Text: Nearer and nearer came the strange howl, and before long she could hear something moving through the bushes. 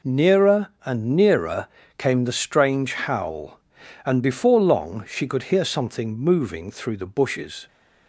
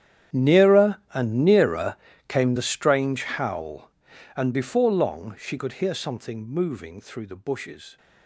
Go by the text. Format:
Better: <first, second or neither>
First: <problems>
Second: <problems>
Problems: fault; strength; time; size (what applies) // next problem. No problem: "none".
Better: first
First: pauses between "nearer" and "came"; slight; at 1.6 s; 0.30 s long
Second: gets quieter; strong; throughout; 20.5 dB // pauses between "nearer" and "came"; slight; at 1.9 s; 0.32 s long